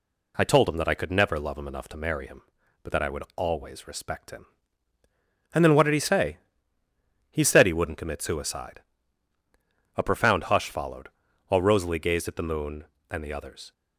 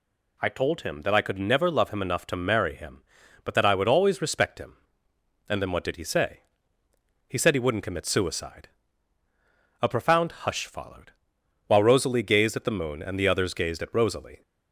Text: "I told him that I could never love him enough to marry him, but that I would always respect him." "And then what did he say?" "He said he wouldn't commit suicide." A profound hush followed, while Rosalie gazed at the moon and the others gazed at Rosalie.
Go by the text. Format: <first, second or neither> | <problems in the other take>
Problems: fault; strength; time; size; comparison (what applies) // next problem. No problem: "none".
second | stops before "gazed at Rosalie"; at 13.7 s